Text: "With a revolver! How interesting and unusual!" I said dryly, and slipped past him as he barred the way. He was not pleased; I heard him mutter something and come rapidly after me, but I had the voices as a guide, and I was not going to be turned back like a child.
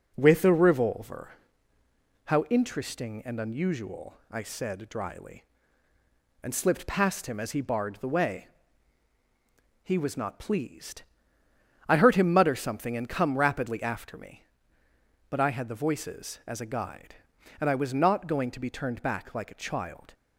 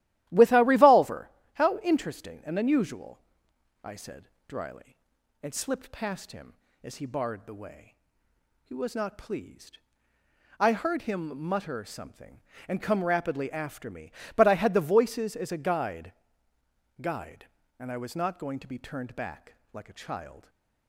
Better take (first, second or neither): first